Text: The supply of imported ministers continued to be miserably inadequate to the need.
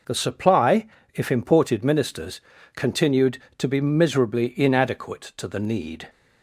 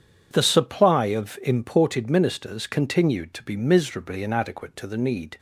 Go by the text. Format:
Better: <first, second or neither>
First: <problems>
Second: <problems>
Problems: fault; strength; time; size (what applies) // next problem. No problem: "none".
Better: second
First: says "if" for "of"; at 1.1 s // pauses between "ministers" and "continued"; slight; at 2.4 s; 0.34 s long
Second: none